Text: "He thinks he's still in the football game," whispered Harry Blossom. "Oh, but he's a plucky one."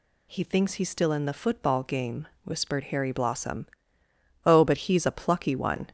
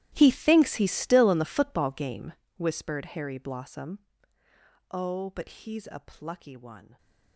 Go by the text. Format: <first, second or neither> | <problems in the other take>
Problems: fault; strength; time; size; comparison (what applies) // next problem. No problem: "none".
first | gets quieter; strong; throughout; 19.5 dB